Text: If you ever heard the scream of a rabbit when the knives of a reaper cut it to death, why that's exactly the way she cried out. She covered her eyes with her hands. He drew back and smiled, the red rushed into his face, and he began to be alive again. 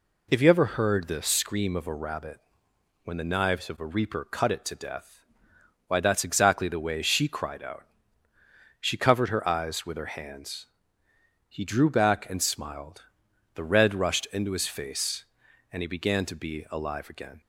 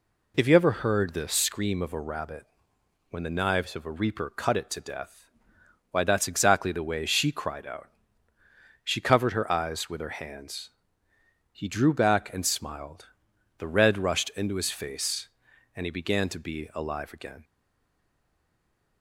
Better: first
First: pauses between "rabbit" and "when"; noticeable; at 2.3 s; 0.64 s long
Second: pauses between "rabbit" and "when"; noticeable; at 2.4 s; 0.64 s long // stays silent after the last word; noticeable; from 17.4 s on; 1.6 s long

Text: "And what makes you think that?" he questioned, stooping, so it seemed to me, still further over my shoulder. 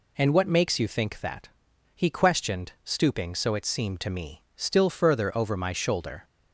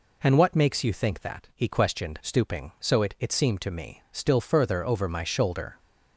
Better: first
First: none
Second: says "it" twice; at 3.1 s

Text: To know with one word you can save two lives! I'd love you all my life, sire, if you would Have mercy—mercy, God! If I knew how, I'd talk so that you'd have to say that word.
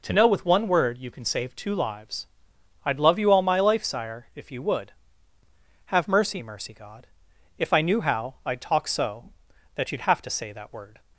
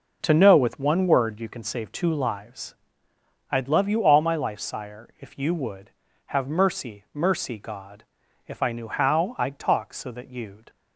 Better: first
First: none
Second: stops before "have to say that word"; at 10.6 s

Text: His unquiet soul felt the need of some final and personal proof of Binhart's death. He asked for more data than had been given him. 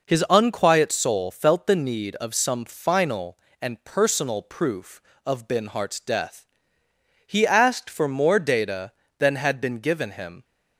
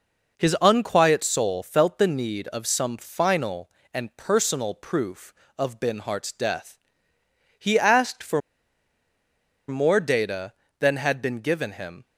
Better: first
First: none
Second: pauses between "for" and "more"; strong; at 8.4 s; 1.2 s long

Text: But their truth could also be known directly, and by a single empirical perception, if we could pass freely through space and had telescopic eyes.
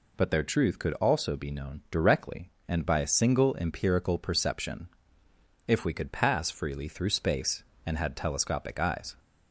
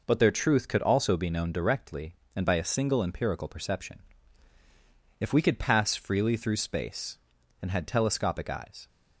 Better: neither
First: none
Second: none

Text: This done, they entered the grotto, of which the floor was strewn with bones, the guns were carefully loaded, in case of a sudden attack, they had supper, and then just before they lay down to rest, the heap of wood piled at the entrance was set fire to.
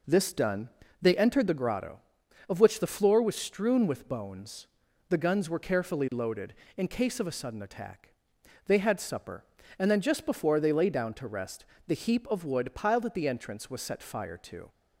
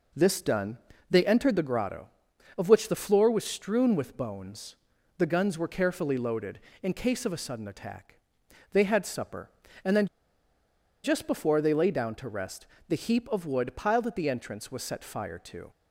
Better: first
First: none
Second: pauses between "then" and "just"; noticeable; at 10.0 s; 0.97 s long

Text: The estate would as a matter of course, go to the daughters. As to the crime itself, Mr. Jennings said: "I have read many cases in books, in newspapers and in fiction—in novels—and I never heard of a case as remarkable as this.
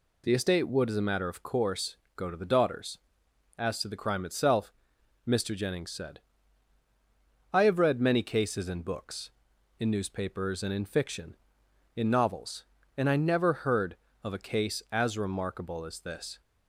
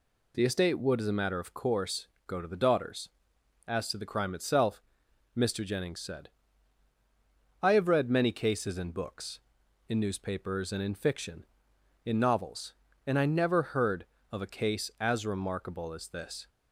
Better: neither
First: none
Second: none

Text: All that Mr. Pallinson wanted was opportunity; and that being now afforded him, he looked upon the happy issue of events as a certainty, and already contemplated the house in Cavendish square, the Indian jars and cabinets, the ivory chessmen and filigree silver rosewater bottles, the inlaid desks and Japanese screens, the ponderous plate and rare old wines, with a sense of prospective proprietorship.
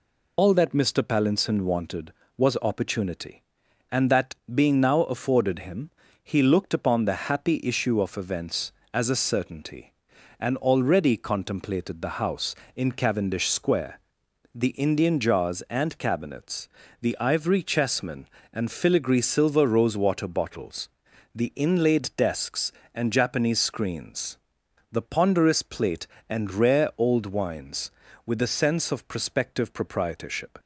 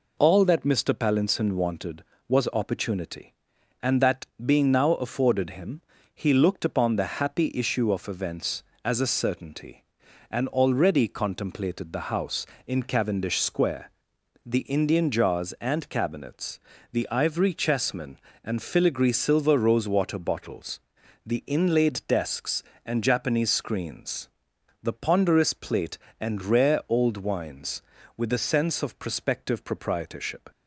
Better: second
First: loses the start of "All"; at 0.3 s; 100 ms // pauses between "that" and "being"; slight; at 4.3 s; 0.18 s long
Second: pauses between "that" and "being"; slight; at 4.2 s; 0.18 s long

